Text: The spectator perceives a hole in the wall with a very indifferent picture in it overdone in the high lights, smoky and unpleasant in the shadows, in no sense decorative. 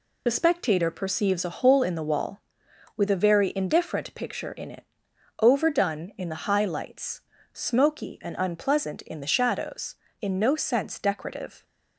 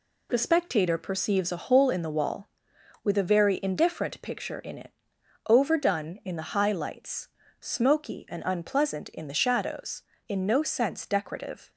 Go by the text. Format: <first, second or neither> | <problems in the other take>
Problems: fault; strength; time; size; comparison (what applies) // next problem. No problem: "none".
second | loses the start of "The"; at 0.2 s; 35 ms // pauses between "it" and "overdone"; noticeable; at 4.8 s; 0.56 s long; noticeable in the second